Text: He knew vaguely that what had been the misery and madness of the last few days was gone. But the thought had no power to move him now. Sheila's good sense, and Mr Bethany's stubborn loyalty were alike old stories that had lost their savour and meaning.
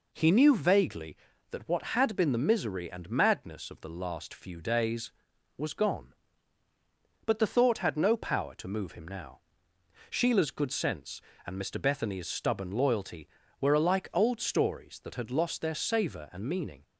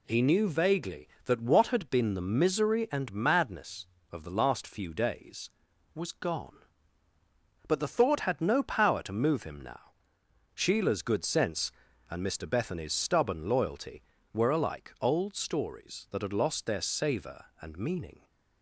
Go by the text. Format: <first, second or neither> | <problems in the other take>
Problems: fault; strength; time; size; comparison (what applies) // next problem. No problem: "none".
neither | none